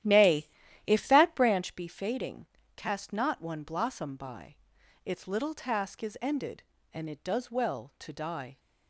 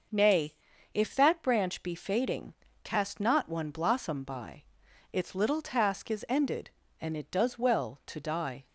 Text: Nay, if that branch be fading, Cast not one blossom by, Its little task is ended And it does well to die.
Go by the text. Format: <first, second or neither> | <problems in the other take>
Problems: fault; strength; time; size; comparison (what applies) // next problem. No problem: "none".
second | starts louder than the rest; strong; until 1.8 s; 12 dB